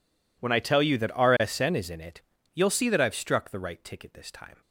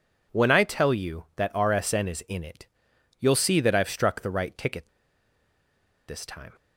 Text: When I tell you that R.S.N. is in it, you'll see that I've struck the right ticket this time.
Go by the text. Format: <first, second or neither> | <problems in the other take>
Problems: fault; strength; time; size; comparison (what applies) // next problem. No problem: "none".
first | pauses between "ticket" and "this"; at 4.8 s; 1.2 s long